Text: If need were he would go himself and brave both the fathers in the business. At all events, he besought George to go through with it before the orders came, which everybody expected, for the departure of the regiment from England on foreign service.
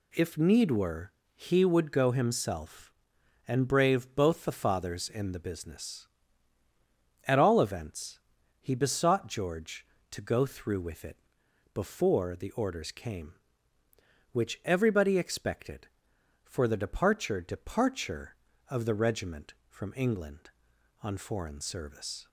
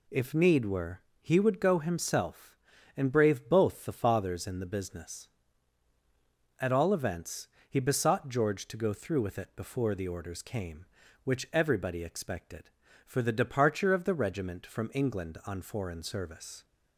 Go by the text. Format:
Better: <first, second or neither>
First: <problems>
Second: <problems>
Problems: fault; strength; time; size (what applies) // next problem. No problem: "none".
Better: second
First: pauses between "were" and "he"; slight; at 1.1 s; 0.22 s long // pauses between "it" and "before"; noticeable; at 11.1 s; 0.56 s long // says "departure" twice; at 17.4 s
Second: pauses between "were" and "he"; slight; at 1.0 s; 0.20 s long